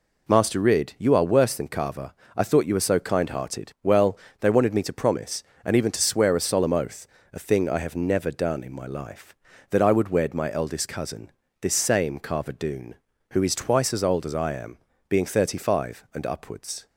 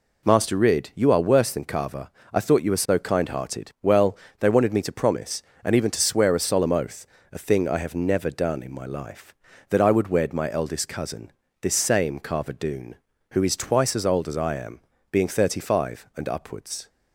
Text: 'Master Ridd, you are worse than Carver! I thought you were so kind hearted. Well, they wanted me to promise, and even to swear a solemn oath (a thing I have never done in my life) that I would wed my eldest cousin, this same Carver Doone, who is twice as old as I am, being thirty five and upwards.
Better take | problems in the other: neither | none

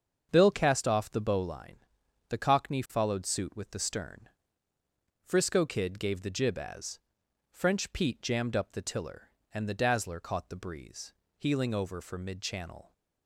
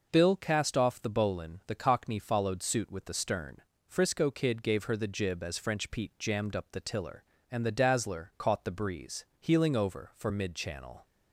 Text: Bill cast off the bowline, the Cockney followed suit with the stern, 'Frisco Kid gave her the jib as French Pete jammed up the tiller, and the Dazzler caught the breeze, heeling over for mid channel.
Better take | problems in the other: second | starts louder than the rest; until 1.3 s; 7 dB // skips "her"; at 6.2 s // pauses between "as" and "French"; noticeable; at 6.9 s; 0.52 s long

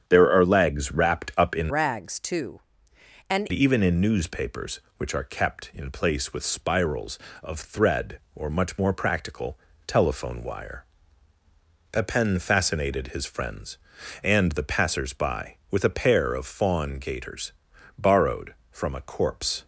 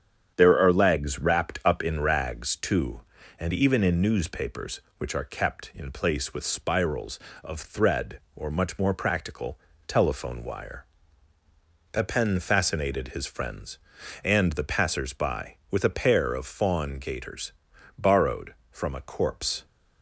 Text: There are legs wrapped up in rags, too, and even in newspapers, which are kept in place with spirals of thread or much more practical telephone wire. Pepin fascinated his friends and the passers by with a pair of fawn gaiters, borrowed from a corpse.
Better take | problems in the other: second | starts louder than the rest; strong; until 1.0 s; 8.5 dB; strong in the second // changes voice from "rags" to "and"; from 1.6 to 3.4 s; 1.8 s long // pauses between "practical" and "telephone"; slight; at 9.5 s; 0.28 s long; slight in the second

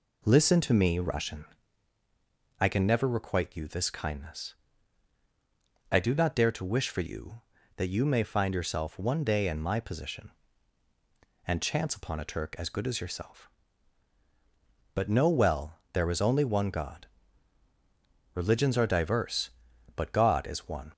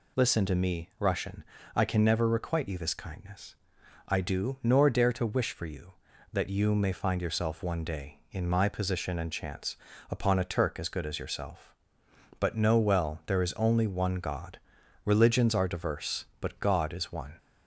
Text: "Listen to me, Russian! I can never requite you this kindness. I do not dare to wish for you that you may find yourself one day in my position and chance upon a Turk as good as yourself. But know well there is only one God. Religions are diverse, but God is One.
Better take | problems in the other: first | says "nor" for "not"; at 4.6 s // pauses between "chance" and "upon"; slight; at 9.7 s; 0.34 s long

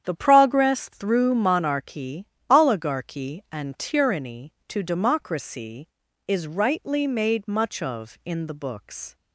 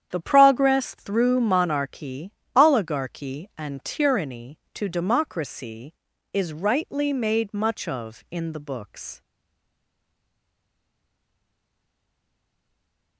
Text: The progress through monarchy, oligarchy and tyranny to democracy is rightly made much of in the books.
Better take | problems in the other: first | starts louder than the rest; strong; until 1.1 s; 9 dB; strong in the first // stays silent after the last word; strong; from 9.2 s on; 3.9 s long

